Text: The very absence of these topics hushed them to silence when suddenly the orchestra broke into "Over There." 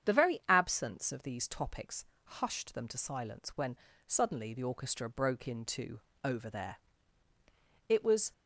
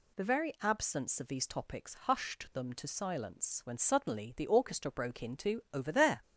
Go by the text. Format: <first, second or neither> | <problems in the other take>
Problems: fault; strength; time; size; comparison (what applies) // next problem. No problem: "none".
second | starts louder than the rest; strong; until 1.1 s; 8 dB // pauses between "topics" and "hushed"; slight; at 2.0 s; 0.22 s long // pauses between "when" and "suddenly"; slight; at 3.7 s; 0.32 s long // pauses between "into" and "Over"; slight; at 5.9 s; 0.24 s long // goes on to say "It was"; slight; from 7.8 s on; 0.42 s long